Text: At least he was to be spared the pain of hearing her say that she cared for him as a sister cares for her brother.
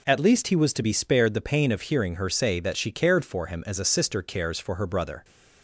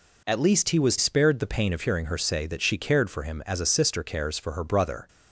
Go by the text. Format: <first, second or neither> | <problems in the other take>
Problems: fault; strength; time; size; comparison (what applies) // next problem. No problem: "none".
first | skips "to be"; at 0.9 s